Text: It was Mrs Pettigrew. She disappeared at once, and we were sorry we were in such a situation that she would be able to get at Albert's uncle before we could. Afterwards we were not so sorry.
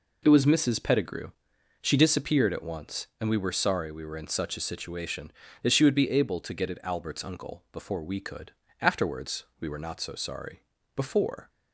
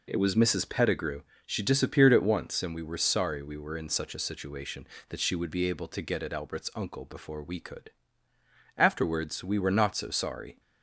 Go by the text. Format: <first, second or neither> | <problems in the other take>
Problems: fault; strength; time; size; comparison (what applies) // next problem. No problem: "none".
second | pauses between "Afterwards" and "we"; slight; at 9.4 s; 0.16 s long // goes on to say "Before"; from 10.9 s on; 0.54 s long